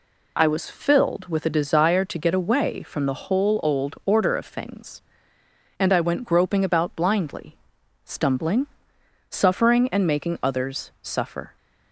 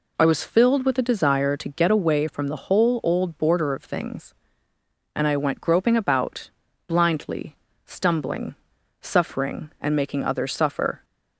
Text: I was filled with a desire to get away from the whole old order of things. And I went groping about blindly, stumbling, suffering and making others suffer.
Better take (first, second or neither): first